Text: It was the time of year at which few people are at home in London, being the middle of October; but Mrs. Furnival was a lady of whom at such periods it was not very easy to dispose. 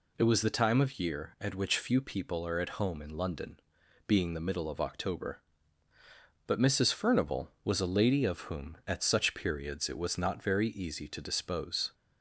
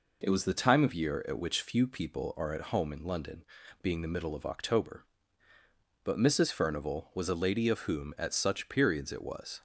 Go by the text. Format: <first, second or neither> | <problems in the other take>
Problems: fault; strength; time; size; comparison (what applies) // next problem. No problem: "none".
first | stops before "not very easy to dispose"; at 9.5 s